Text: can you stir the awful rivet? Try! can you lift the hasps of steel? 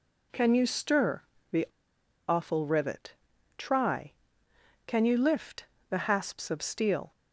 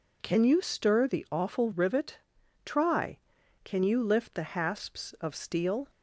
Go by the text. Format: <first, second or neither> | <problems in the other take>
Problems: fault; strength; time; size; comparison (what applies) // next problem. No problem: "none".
second | pauses between "stir" and "the"; slight; at 1.2 s; 0.28 s long // pauses between "the" and "awful"; noticeable; at 1.6 s; 0.63 s long // pauses between "lift" and "the"; slight; at 5.6 s; 0.24 s long